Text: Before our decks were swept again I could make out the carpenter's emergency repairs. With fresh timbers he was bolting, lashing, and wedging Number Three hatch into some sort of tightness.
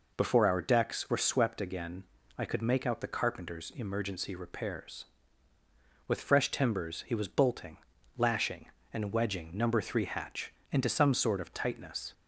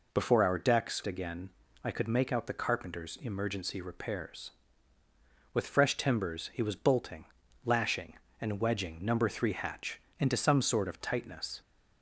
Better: first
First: pauses between "again" and "I"; slight; at 2.0 s; 0.34 s long // pauses between "hatch" and "into"; slight; at 10.5 s; 0.18 s long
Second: skips "were swept"; at 1.0 s // pauses between "again" and "I"; slight; at 1.4 s; 0.34 s long // pauses between "hatch" and "into"; slight; at 9.9 s; 0.18 s long

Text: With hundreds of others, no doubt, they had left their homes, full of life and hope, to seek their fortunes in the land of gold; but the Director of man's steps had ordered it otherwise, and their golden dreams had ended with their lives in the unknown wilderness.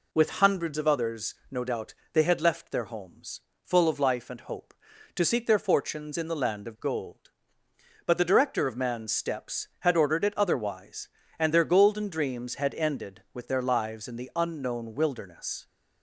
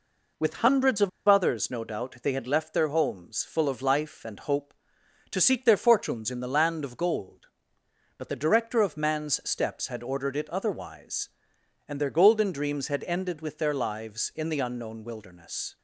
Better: first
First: none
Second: pauses between "of" and "others"; slight; at 1.0 s; 0.19 s long

